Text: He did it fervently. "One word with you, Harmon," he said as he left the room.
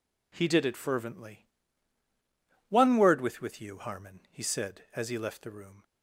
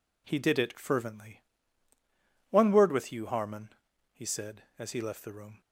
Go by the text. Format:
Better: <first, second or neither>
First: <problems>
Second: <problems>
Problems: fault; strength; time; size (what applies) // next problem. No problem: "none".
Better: second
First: says "with" twice; at 3.3 s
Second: none